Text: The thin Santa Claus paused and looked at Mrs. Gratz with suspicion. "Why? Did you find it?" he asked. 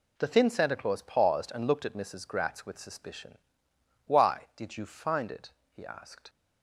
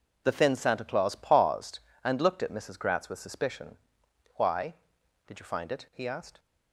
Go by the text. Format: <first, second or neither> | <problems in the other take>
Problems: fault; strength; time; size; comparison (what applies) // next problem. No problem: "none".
neither | none